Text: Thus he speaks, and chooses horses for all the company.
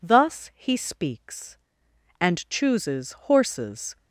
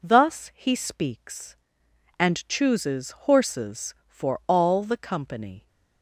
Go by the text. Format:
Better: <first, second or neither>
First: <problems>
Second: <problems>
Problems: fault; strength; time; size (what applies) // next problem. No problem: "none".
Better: second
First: stops before "for all the company"; at 3.9 s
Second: none